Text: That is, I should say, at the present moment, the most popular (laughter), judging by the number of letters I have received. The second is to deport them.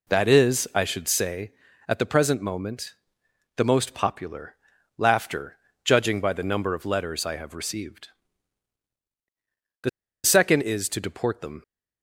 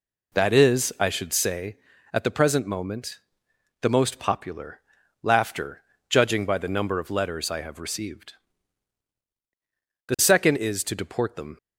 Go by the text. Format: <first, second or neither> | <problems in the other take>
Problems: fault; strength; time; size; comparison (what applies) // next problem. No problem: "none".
second | pauses between "The" and "second"; slight; at 9.8 s; 0.34 s long